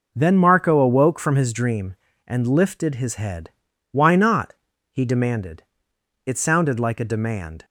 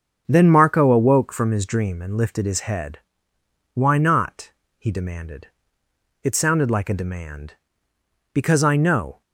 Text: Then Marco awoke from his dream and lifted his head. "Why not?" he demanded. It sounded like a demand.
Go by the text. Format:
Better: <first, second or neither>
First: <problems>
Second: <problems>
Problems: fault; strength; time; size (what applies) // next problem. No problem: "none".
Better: first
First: none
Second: starts louder than the rest; until 1.2 s; 6.5 dB // goes on to say "Because I know"; noticeable; from 8.3 s on; 0.88 s long